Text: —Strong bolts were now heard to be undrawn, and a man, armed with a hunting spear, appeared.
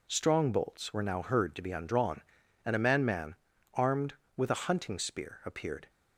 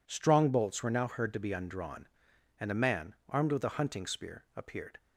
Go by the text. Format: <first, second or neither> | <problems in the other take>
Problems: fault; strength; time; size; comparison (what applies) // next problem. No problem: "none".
second | says "man" twice; at 3.0 s